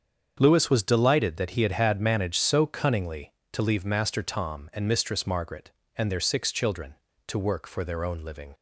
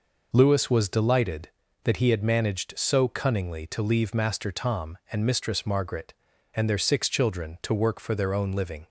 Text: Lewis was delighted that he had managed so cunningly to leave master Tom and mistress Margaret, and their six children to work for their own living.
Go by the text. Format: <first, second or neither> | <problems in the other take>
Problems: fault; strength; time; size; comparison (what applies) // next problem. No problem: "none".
second | starts louder than the rest; strong; until 1.4 s; 7 dB // says "had" twice; at 1.7 s